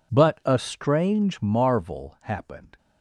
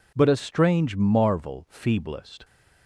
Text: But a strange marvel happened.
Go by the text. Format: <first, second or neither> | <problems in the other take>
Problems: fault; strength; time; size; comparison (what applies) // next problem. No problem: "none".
first | says "feeblest" for "happened"; at 1.7 s